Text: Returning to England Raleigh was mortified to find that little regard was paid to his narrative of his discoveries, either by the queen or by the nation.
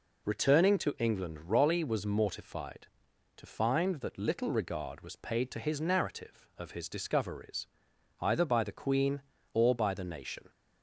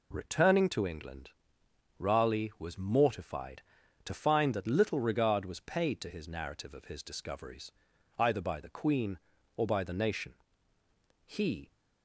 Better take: first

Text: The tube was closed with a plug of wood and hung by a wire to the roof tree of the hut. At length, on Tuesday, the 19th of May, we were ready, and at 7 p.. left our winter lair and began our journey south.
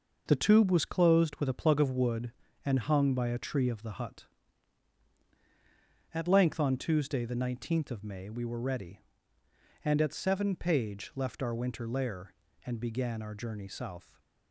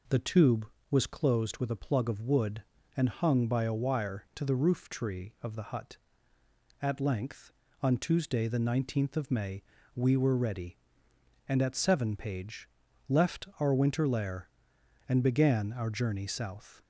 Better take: second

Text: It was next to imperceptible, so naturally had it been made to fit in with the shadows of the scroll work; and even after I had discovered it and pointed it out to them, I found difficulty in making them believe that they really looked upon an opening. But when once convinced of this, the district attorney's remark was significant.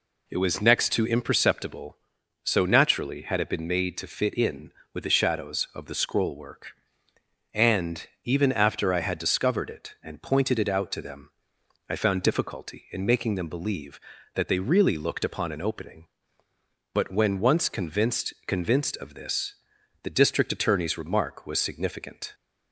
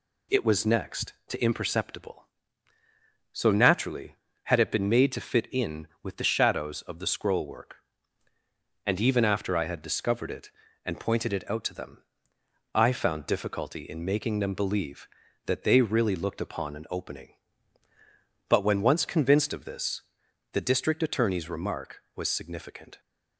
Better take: second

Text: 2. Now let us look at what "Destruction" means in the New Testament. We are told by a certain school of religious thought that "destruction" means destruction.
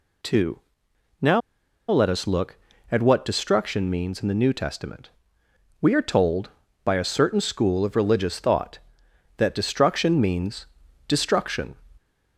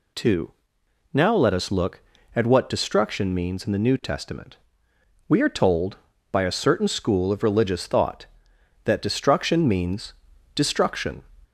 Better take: second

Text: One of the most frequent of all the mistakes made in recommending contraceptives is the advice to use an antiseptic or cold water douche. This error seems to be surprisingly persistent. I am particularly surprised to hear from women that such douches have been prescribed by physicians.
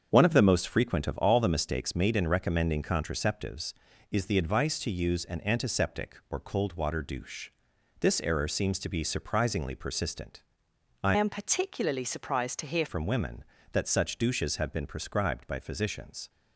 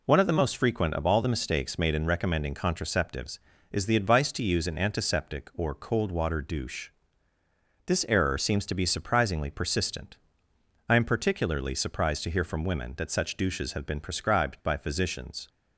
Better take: second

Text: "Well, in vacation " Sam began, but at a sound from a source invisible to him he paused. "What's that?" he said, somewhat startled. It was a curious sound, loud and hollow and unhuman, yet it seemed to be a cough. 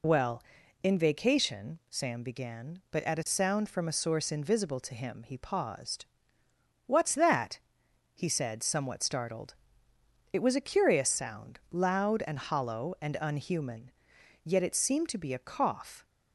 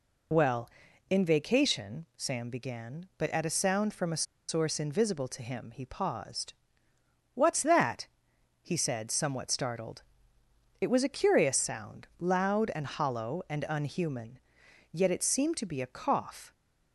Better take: first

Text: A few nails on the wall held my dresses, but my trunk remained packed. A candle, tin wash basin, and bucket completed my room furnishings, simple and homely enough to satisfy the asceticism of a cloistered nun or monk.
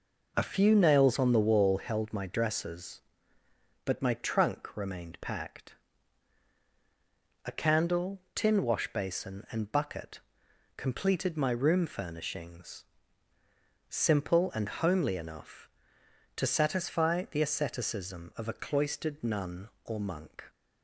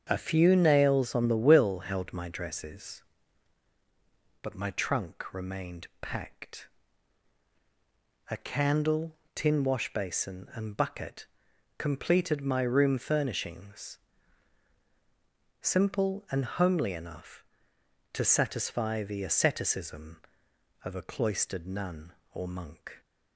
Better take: first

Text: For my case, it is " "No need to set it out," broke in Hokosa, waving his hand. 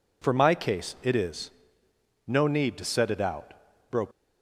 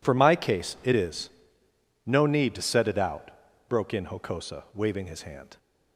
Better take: second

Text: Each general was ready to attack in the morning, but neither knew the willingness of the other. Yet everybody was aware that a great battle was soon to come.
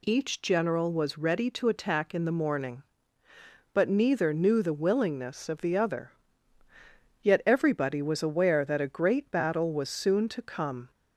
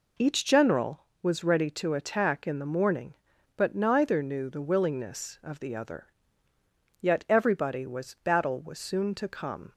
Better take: first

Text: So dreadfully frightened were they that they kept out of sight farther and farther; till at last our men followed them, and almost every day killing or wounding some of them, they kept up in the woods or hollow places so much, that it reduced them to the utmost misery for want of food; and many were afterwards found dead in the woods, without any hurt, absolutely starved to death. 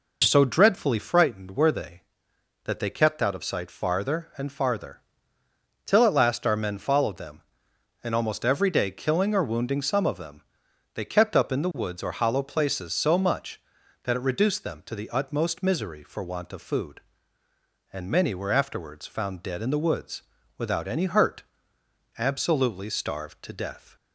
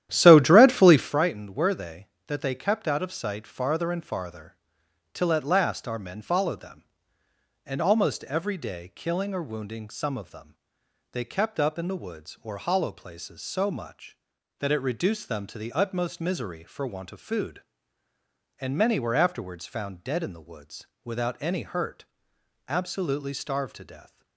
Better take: first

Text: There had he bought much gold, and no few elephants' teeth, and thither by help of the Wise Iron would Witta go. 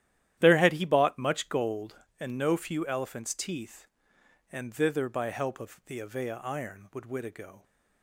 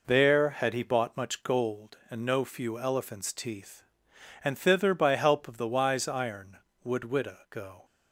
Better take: second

